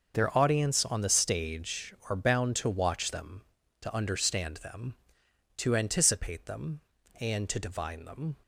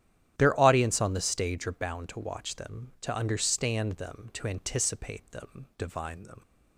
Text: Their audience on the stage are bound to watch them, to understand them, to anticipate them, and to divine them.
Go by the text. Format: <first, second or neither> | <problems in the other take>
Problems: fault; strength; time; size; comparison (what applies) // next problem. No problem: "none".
first | starts louder than the rest; strong; until 1.4 s; 11 dB; noticeable in the first // skips "and to"; at 5.7 s